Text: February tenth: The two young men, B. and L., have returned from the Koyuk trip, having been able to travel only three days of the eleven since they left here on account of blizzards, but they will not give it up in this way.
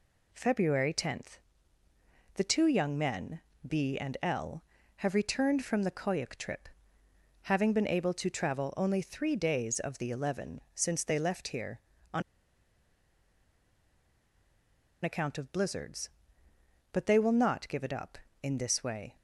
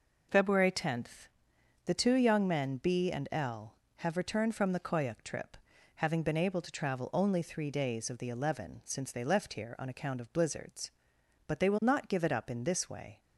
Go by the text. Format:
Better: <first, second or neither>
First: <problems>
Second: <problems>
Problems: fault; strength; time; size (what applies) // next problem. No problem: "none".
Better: second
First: pauses between "on" and "account"; strong; at 12.2 s; 2.8 s long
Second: none